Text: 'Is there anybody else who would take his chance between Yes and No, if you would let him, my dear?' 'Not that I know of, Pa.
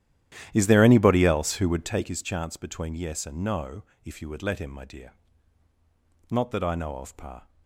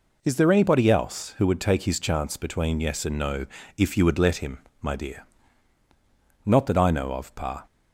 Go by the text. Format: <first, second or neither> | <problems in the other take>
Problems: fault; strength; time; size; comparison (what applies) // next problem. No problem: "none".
second | starts louder than the rest; strong; until 2.1 s; 12 dB